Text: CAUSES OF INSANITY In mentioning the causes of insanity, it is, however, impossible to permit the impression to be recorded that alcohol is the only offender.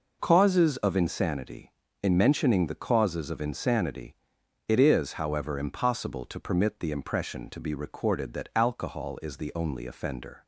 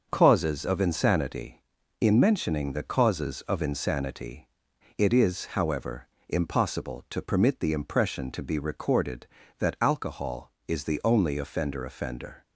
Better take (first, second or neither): first